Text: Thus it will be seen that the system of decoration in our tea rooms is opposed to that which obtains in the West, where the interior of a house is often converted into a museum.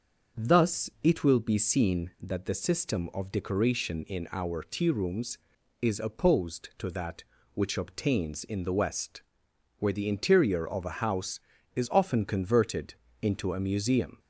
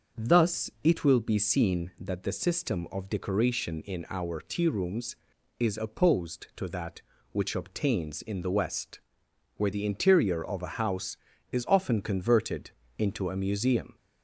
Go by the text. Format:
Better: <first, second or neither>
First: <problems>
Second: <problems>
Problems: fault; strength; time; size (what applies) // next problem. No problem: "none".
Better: neither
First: starts louder than the rest; until 1.4 s; 6.5 dB // pauses between "converted" and "into"; slight; at 12.9 s; 0.28 s long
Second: starts louder than the rest; until 1.3 s; 6.5 dB // pauses between "converted" and "into"; slight; at 12.7 s; 0.28 s long